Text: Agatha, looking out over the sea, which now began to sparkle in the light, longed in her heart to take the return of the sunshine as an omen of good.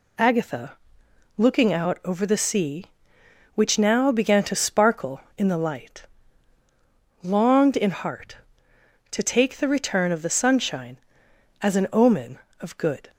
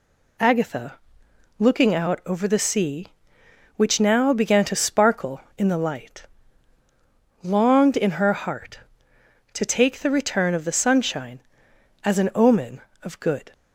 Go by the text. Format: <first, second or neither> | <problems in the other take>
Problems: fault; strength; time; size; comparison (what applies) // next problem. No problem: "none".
second | skips "her"; at 7.9 s